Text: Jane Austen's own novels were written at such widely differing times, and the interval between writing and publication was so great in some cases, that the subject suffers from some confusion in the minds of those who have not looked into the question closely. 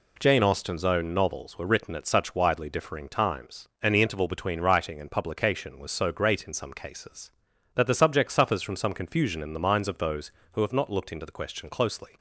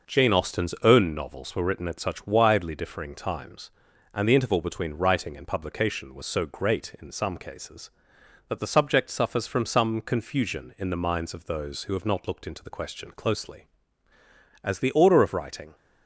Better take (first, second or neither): first